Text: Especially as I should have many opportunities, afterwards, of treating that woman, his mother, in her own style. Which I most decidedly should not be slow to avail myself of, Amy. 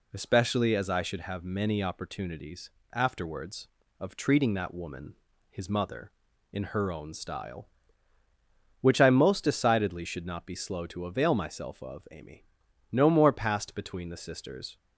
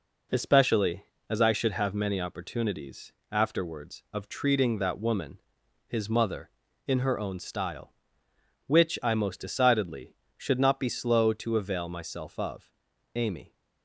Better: second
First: goes on to say "No more passed between the sisters"; strong; from 12.9 s on; 1.8 s long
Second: none

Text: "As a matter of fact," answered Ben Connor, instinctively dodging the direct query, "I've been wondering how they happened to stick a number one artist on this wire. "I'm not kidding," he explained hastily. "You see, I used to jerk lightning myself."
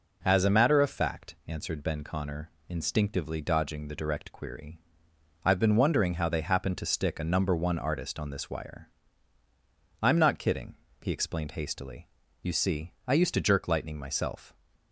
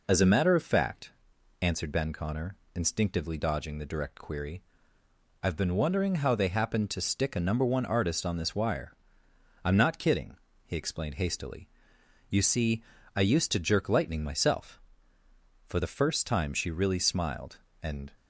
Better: first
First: none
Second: goes on to say "For the first time she really smiled and"; strong; from 15.6 s on; 2.4 s long

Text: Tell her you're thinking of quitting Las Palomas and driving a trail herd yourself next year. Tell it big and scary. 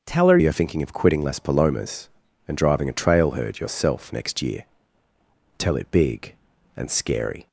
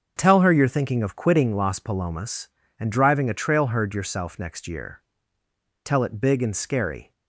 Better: second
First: starts louder than the rest; until 1.0 s; 6.5 dB // changes voice at "you're"; from 0.3 s on; 7.1 s long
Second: starts louder than the rest; until 1.1 s; 6.5 dB

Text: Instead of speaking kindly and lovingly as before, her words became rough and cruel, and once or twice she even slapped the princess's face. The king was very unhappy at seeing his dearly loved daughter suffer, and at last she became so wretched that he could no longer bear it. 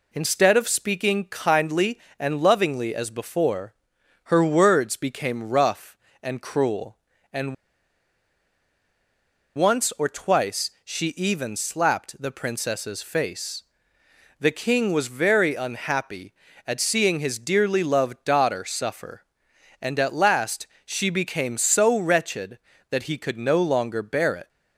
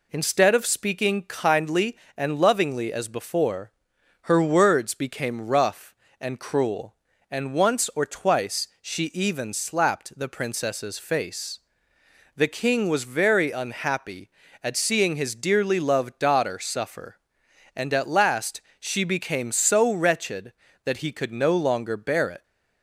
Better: second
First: pauses between "and" and "once"; strong; at 7.5 s; 2.0 s long // pauses between "last" and "she"; slight; at 20.6 s; 0.18 s long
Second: pauses between "last" and "she"; slight; at 18.6 s; 0.18 s long

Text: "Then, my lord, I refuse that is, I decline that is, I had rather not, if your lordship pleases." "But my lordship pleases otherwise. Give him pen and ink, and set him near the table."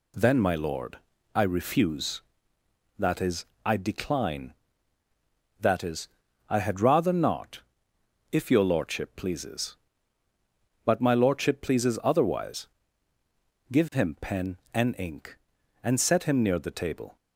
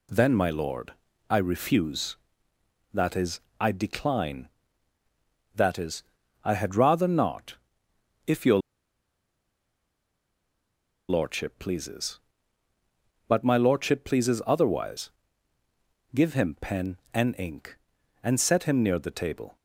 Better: first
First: none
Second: pauses between "your" and "lordship"; strong; at 8.5 s; 2.5 s long

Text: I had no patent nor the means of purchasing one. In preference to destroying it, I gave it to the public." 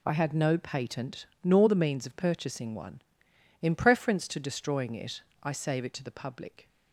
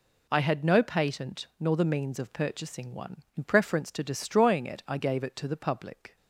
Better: second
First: pauses between "patent" and "nor"; slight; at 1.2 s; 0.16 s long // says "save" for "gave"; at 5.5 s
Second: none

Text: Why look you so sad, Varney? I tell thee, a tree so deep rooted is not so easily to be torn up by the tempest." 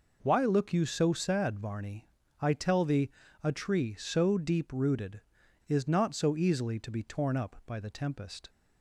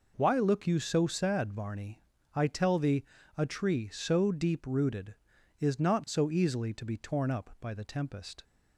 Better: neither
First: none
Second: none

